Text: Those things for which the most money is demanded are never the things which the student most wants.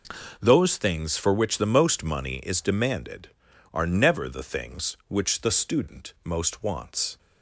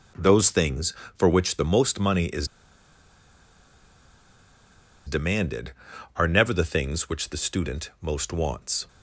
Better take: first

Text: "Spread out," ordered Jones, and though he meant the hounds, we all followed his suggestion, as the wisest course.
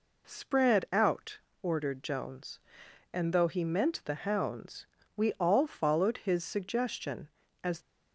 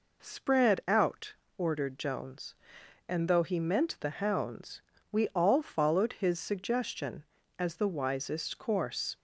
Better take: second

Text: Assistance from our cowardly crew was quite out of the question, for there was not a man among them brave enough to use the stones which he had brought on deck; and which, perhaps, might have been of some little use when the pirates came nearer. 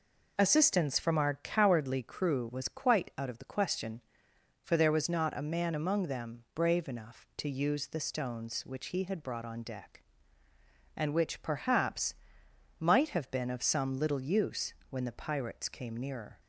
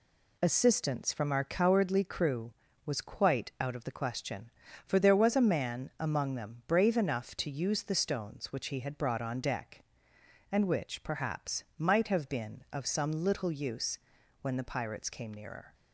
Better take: first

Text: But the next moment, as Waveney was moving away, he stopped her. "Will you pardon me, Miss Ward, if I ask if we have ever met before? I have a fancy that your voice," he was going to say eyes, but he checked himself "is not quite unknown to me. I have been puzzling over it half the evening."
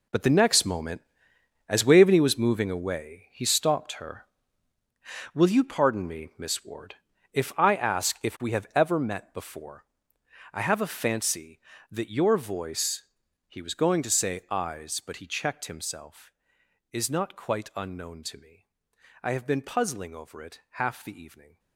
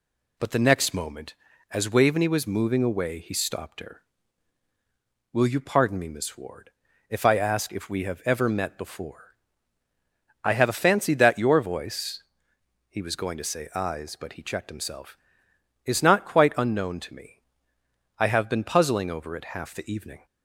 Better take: second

